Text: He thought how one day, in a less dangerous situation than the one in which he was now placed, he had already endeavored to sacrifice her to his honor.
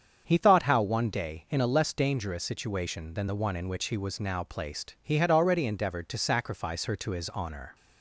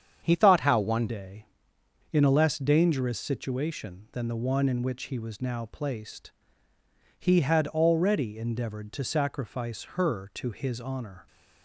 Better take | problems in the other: first | starts louder than the rest; strong; until 1.2 s; 8 dB; strong in the first // changes voice at "day"; from 1.0 s on; 10.2 s long

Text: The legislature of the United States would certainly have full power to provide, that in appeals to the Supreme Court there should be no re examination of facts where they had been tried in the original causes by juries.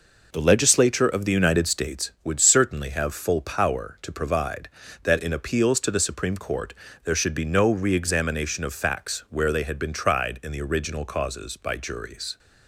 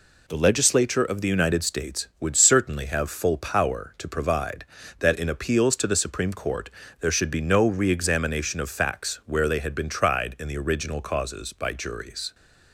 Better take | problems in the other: second | starts louder than the rest; noticeable; until 2.2 s; 5 dB // pauses between "Court" and "there"; slight; at 6.7 s; 0.30 s long; slight in the second

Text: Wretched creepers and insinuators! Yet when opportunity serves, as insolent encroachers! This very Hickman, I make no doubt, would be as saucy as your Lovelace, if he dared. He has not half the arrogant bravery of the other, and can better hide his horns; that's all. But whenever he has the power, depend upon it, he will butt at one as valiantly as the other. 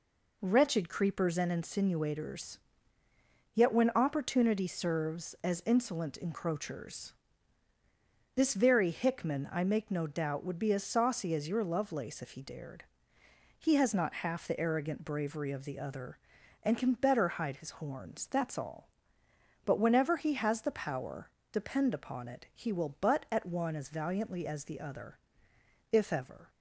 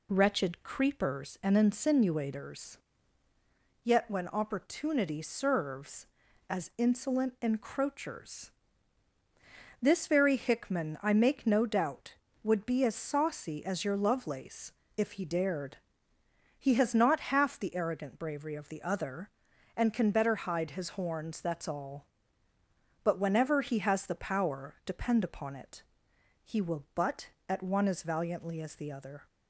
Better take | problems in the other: second | goes on to say "If ever"; from 25.9 s on; 0.56 s long

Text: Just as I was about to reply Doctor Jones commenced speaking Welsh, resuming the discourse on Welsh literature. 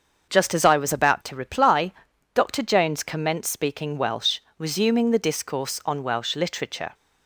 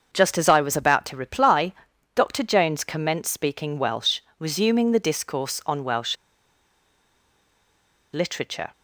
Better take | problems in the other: first | starts louder than the rest; until 1.1 s; 6.5 dB; also in the first // pauses between "reply" and "Doctor"; at 1.7 s; 0.42 s long; also in the first // pauses between "Welsh" and "literature"; strong; at 6.1 s; 1.9 s long

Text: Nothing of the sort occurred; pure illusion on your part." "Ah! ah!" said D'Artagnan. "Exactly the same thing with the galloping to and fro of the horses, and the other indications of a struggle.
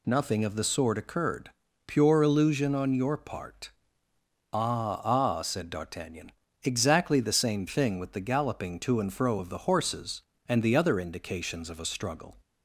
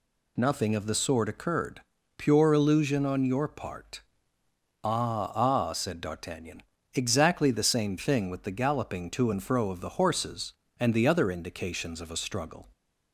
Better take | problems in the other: neither | none

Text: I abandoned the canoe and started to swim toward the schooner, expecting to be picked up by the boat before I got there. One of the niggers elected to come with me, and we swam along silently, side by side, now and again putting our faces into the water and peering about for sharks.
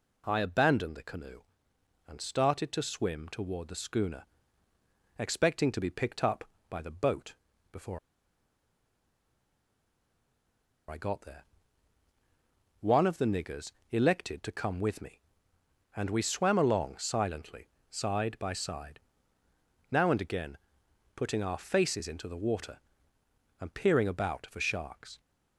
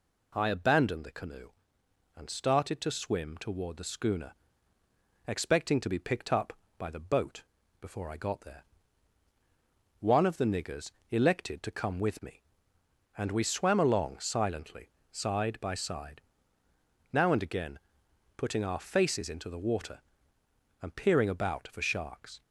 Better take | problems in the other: second | pauses between "boat" and "before"; slight; at 7.3 s; 0.36 s long; slight in the second // pauses between "before" and "I"; strong; at 7.9 s; 2.9 s long // pauses between "niggers" and "elected"; slight; at 13.6 s; 0.22 s long; slight in the second // pauses between "again" and "putting"; noticeable; at 20.5 s; 0.56 s long; noticeable in the second

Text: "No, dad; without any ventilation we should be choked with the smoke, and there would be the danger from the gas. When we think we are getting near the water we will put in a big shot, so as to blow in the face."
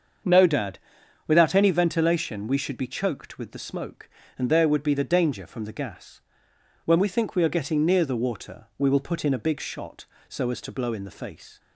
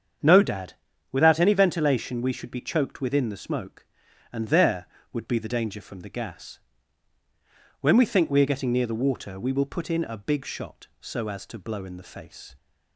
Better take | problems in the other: first | starts louder than the rest; strong; until 1.6 s; 7.5 dB; also in the first // says "within" for "with"; at 2.9 s

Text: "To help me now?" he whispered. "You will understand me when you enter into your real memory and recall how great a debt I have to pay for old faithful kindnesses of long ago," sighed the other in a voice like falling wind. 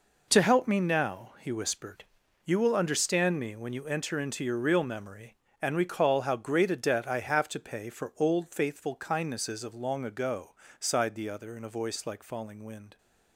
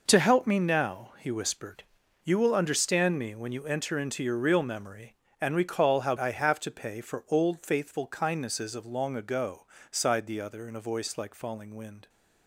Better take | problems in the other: first | skips "great a debt"; at 6.1 s

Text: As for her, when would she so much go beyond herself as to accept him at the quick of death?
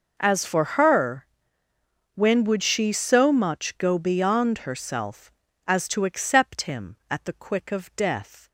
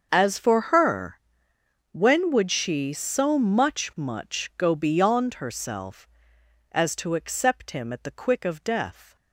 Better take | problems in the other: first | starts louder than the rest; until 1.1 s; 6.5 dB // says "much" twice; at 3.9 s

